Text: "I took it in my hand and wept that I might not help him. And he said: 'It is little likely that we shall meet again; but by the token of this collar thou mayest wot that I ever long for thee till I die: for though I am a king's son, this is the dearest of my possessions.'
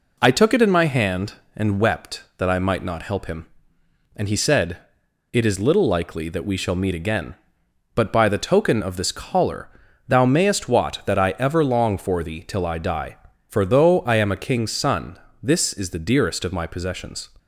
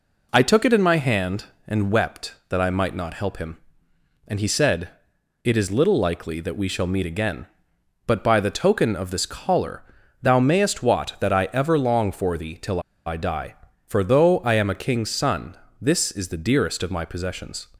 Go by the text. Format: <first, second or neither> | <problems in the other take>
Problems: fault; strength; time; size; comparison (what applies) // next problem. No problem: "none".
first | pauses between "collar" and "thou"; at 9.8 s; 0.40 s long; also in the first // pauses between "till" and "I"; slight; at 12.7 s; 0.27 s long